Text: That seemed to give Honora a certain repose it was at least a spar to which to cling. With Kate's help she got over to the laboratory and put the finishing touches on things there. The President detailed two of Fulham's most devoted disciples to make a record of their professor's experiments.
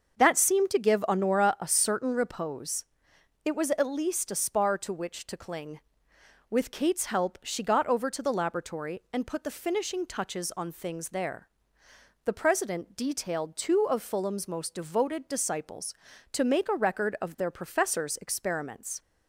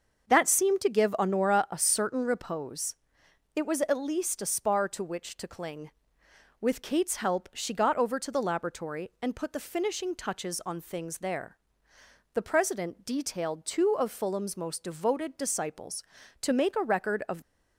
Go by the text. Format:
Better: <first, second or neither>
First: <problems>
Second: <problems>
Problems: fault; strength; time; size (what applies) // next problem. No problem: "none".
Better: first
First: starts louder than the rest; until 1.2 s; 6.5 dB // pauses between "repose" and "it"; noticeable; at 2.8 s; 0.60 s long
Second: starts louder than the rest; until 1.3 s; 6.5 dB // pauses between "repose" and "it"; noticeable; at 2.9 s; 0.60 s long // stops before "their professor's experiments"; at 17.4 s